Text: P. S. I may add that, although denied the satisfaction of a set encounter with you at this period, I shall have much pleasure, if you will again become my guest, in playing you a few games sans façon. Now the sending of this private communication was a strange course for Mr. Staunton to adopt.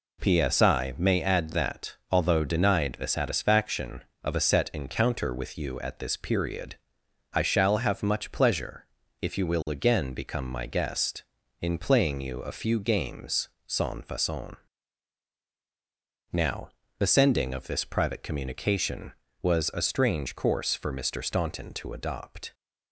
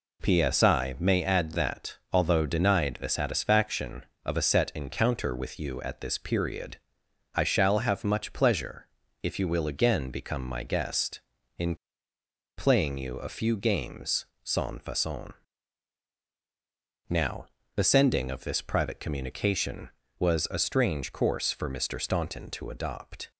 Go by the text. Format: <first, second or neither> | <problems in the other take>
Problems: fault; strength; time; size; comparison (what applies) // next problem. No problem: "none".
first | pauses between "in" and "playing"; noticeable; at 11.7 s; 0.82 s long // pauses between "games" and "sans"; slight; at 14.2 s; 0.16 s long; slight in the first // pauses between "Now" and "the"; slight; at 17.4 s; 0.30 s long; slight in the first